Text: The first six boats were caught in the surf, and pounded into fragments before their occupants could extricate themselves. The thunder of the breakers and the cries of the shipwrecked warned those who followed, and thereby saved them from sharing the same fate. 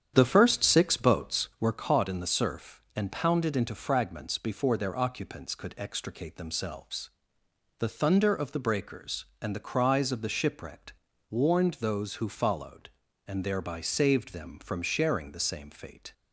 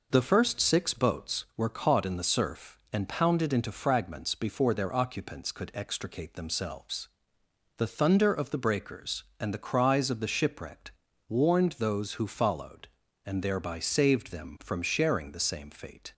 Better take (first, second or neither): second